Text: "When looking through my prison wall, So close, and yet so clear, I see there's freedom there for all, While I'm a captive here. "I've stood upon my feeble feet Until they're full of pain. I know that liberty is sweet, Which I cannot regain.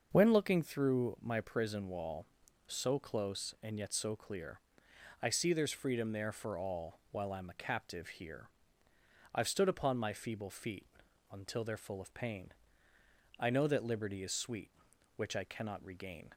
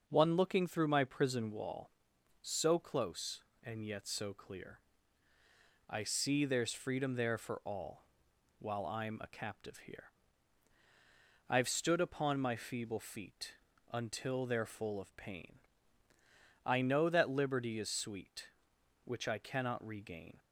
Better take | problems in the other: first | starts louder than the rest; until 1.0 s; 6.5 dB; also in the first // says "One" for "When"; at 0.0 s // pauses between "feet" and "Until"; slight; at 13.5 s; 0.36 s long; also in the first

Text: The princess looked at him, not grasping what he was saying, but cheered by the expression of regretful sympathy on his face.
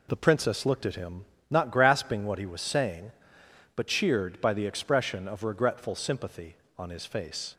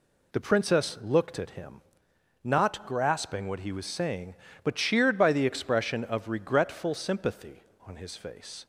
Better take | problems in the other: neither | none

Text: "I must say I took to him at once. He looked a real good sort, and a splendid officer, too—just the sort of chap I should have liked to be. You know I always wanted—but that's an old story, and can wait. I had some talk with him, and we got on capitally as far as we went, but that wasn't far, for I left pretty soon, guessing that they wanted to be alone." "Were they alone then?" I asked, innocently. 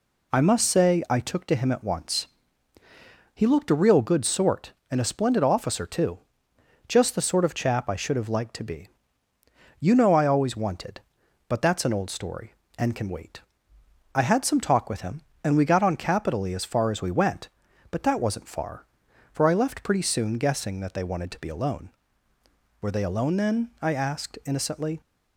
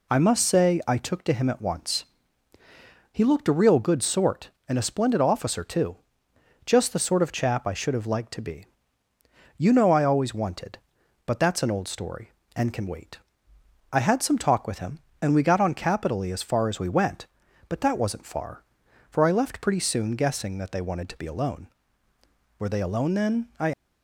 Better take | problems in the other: first | stops before "asked innocently"; at 23.7 s

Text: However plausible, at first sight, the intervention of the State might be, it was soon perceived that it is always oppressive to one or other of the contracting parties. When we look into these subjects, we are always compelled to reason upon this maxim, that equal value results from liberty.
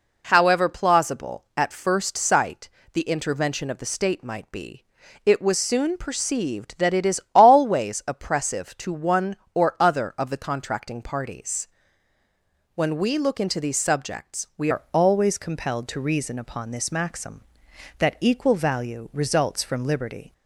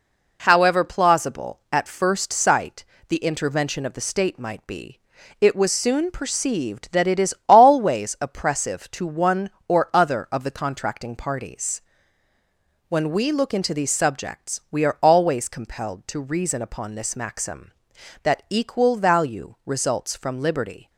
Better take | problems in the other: second | changes voice at "are"; from 14.7 s on; 5.6 s long

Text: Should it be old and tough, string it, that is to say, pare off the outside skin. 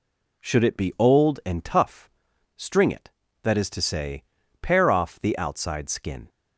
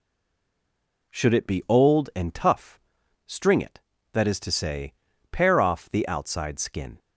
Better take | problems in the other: first | stays silent before the first word; until 1.1 s; 1.1 s long

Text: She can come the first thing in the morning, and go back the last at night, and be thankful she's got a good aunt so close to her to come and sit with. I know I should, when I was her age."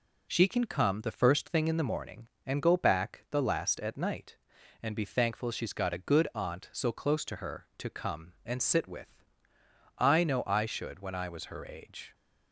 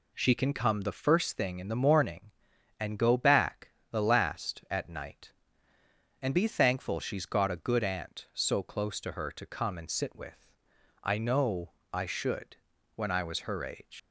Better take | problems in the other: first | pauses between "back" and "the"; slight; at 3.7 s; 0.18 s long // pauses between "know" and "I"; slight; at 11.7 s; 0.20 s long // leaves "age" unfinished; at 13.9 s; 135 ms

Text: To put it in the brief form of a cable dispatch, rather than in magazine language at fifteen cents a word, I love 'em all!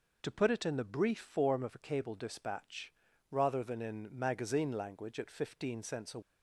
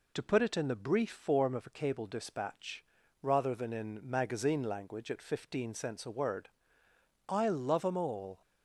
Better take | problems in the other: second | stops before "word I love em all"; at 6.2 s

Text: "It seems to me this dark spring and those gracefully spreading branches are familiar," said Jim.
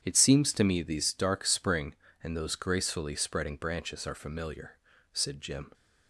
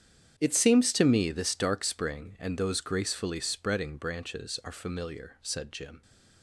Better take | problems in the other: second | starts louder than the rest; strong; until 1.0 s; 8.5 dB; strong in the second // says "these" for "this"; at 0.8 s

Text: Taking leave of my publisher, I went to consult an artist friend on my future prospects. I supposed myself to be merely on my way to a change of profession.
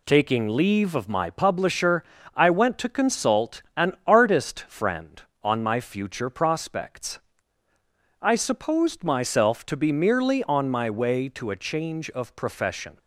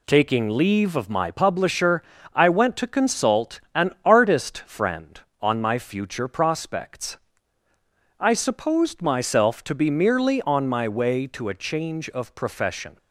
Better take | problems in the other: neither | none

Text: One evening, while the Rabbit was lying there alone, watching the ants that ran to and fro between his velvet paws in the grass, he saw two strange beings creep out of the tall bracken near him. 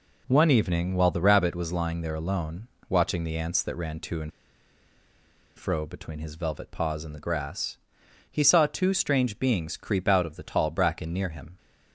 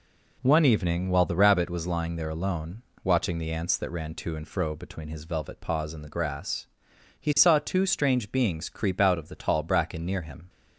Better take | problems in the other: second | pauses between "and" and "fro"; strong; at 4.3 s; 1.2 s long

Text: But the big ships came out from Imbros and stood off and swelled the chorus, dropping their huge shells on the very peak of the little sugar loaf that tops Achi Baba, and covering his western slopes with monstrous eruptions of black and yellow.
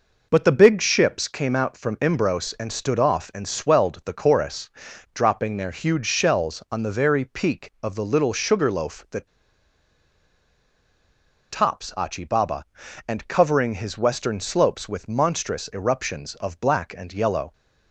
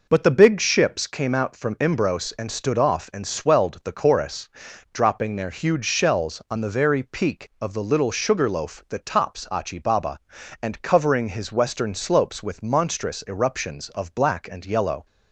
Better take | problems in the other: second | pauses between "that" and "tops"; strong; at 9.2 s; 2.2 s long

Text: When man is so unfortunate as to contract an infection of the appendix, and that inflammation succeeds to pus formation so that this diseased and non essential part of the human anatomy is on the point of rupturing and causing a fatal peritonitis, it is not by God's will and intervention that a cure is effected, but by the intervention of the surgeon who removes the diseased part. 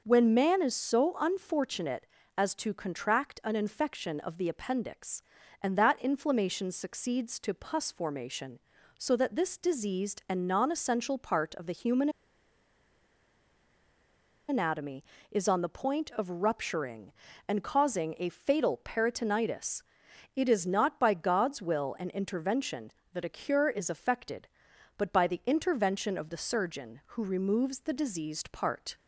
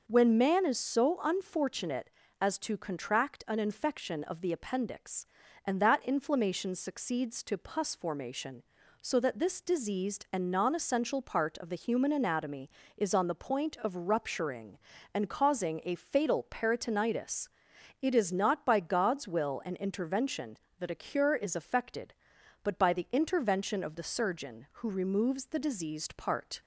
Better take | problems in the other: second | pauses between "human" and "anatomy"; strong; at 12.0 s; 2.3 s long

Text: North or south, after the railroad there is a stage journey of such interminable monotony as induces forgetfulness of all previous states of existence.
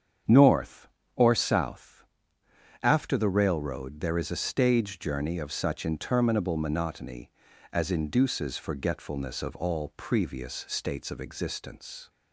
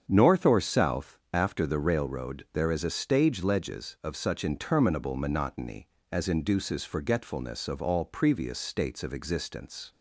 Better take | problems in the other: first | starts louder than the rest; strong; until 1.0 s; 7.5 dB; strong in the first // says "ledges" for "journey"; at 3.4 s

